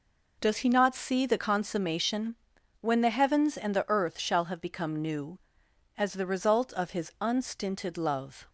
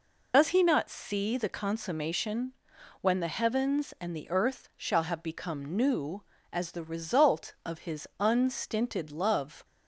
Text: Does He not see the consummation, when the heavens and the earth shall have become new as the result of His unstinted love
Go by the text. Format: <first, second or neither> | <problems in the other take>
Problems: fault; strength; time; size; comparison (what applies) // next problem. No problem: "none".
first | loses the start of "Does"; at 0.3 s; 80 ms